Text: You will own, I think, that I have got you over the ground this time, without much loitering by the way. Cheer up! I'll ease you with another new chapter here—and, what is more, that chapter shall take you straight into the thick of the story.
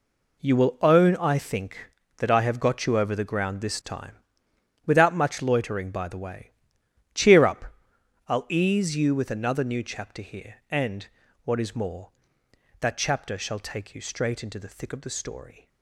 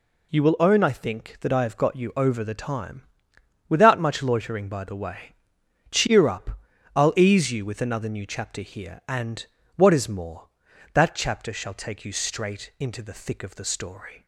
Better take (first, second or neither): first